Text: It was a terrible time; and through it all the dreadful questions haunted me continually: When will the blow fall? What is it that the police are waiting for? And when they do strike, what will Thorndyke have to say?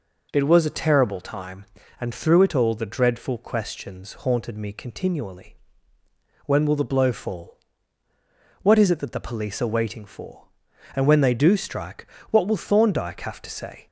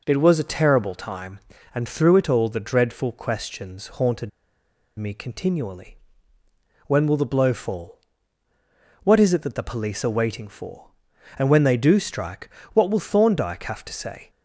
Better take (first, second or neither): first